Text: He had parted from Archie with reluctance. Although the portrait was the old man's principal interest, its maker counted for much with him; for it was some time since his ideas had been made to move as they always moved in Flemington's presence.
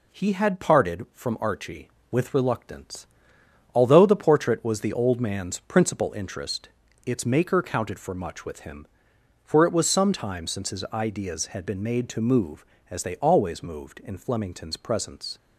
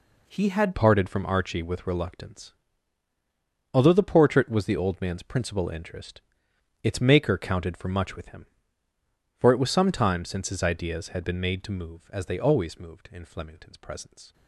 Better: first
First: none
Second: changes voice at "parted"; from 0.7 s on; 13.6 s long

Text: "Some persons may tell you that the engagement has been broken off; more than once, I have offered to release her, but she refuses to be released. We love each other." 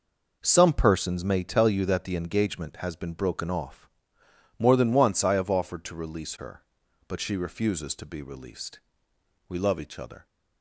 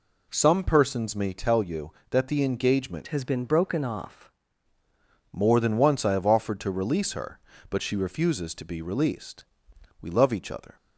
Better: first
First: none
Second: changes voice from "has" to "off"; from 3.0 to 4.3 s; 1.3 s long

